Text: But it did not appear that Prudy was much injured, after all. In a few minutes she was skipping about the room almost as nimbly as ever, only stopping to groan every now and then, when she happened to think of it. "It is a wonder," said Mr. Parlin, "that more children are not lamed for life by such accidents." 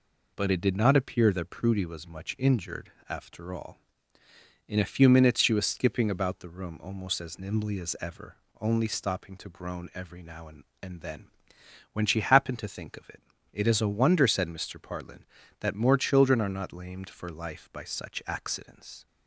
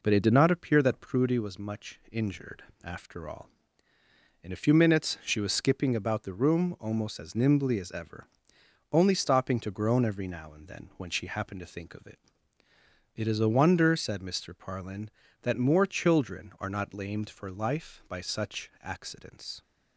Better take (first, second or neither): second